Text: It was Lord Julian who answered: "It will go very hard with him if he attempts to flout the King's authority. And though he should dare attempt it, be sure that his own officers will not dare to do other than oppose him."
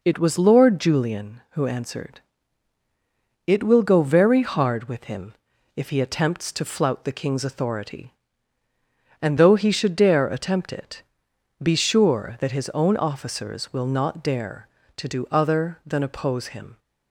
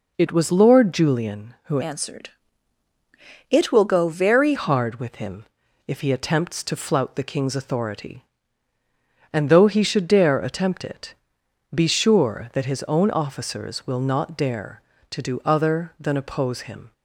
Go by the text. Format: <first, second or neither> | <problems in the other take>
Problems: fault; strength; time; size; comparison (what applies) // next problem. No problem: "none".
first | changes voice from "answered" to "very"; from 1.8 to 4.5 s; 2.7 s long // pauses between "him" and "if"; at 5.4 s; 0.40 s long; also in the first